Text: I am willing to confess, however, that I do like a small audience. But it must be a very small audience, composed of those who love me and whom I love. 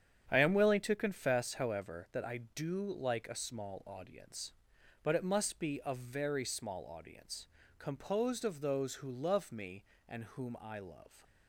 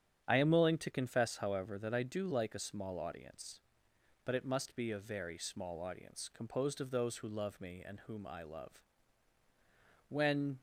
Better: first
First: starts louder than the rest; strong; until 1.2 s; 8.5 dB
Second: starts louder than the rest; strong; until 1.2 s; 9 dB // goes on to say "When"; from 10.0 s on; 0.50 s long

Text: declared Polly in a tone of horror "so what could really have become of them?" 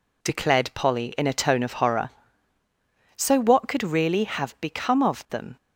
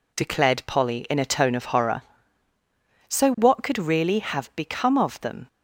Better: neither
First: none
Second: none

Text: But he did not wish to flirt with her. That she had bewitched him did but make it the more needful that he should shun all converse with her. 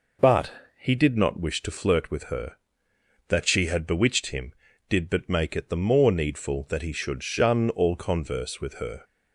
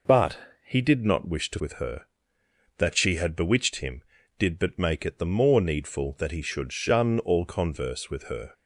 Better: first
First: pauses between "But" and "he"; slight; at 0.5 s; 0.26 s long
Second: pauses between "But" and "he"; slight; at 0.3 s; 0.26 s long // skips "flirt"; at 1.5 s

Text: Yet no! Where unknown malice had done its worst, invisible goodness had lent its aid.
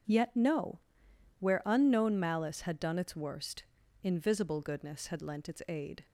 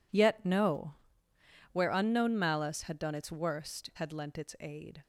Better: first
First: none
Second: skips "invisible goodness"; at 3.9 s

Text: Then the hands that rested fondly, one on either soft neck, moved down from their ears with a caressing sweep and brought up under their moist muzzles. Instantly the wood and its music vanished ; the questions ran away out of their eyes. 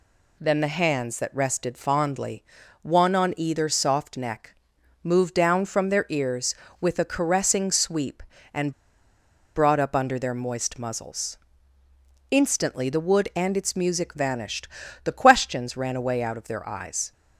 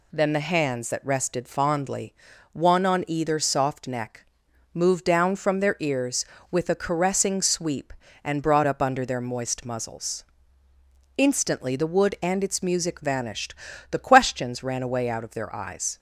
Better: second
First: pauses between "and" and "brought"; noticeable; at 8.7 s; 0.85 s long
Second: none

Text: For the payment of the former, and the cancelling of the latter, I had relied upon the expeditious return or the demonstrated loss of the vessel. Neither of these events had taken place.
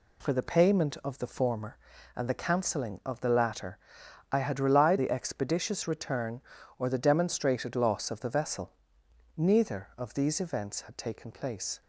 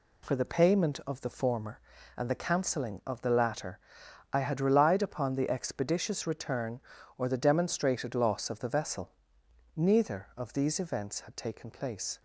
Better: second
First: skips "upon"; at 4.9 s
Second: none

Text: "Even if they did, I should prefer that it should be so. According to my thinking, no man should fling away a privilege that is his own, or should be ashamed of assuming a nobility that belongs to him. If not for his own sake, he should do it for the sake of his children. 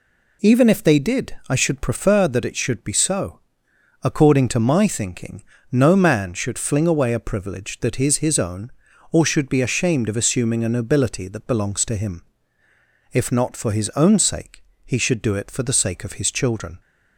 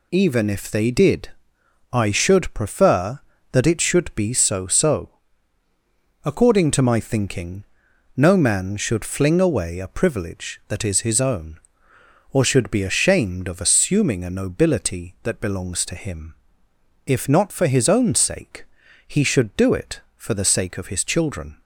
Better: first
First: none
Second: says "so" twice; at 4.6 s

